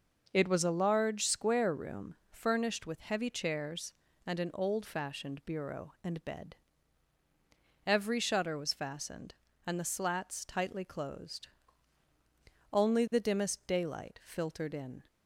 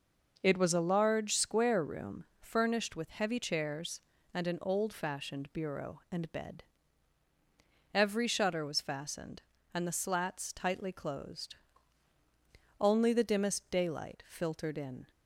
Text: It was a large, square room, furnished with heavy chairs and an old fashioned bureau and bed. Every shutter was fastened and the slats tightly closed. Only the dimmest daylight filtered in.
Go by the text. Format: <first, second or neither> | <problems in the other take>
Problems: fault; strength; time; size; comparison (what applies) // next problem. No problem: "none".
neither | none